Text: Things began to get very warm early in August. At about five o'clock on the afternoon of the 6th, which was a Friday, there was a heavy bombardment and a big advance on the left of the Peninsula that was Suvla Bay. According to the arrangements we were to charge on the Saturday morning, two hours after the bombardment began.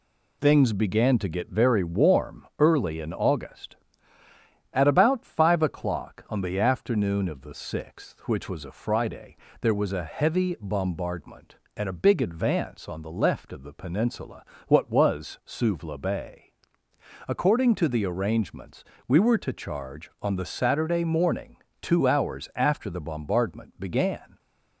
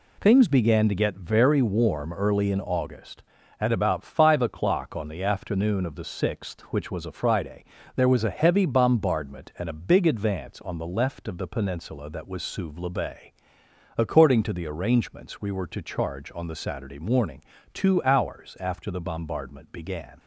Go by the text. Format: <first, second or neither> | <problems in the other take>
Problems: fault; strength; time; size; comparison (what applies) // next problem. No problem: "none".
second | says "what" for "that"; at 14.6 s // pauses between "arrangements" and "we"; slight; at 18.8 s; 0.24 s long